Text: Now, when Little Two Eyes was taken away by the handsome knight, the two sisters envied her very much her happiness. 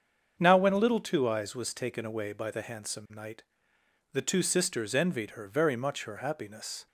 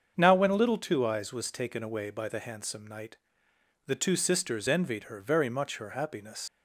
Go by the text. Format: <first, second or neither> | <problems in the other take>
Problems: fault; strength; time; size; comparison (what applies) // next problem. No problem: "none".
first | starts louder than the rest; until 1.1 s; 7 dB; also in the first // leaves "happiness" unfinished; at 6.4 s; 120 ms